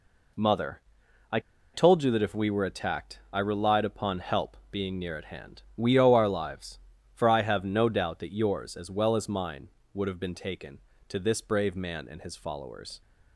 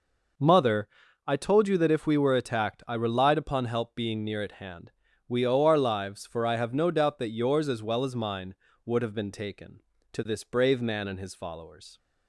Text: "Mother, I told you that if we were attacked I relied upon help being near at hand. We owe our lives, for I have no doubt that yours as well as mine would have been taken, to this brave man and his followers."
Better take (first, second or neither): second